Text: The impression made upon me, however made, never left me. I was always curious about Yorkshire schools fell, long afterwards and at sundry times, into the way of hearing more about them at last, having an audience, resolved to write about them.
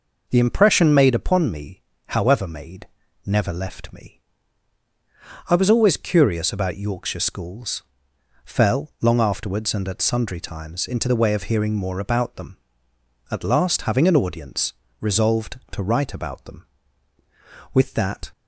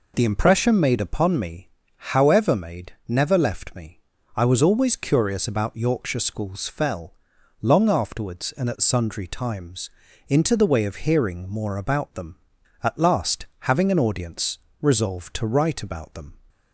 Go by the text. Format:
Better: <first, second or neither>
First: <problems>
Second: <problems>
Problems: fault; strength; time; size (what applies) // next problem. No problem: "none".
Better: second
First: pauses between "schools" and "fell"; noticeable; at 7.8 s; 0.60 s long // goes on to say "With that"; from 17.7 s on; 0.58 s long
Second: none